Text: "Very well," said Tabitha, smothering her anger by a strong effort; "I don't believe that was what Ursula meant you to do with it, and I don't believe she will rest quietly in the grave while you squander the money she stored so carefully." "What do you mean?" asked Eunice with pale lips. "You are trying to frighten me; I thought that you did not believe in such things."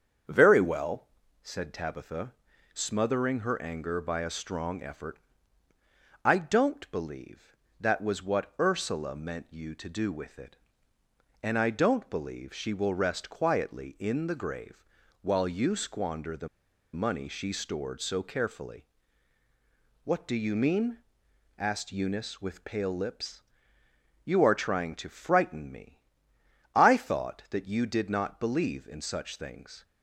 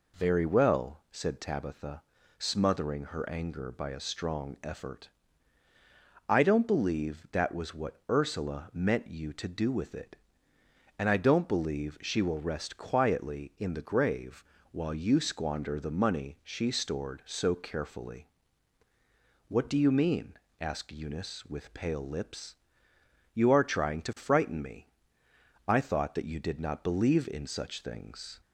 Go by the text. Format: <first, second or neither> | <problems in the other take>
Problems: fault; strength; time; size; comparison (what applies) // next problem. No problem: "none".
second | starts louder than the rest; strong; until 1.6 s; 7 dB // pauses between "grave" and "while"; at 14.8 s; 0.38 s long; slight in the second // pauses between "the" and "money"; at 16.4 s; 0.45 s long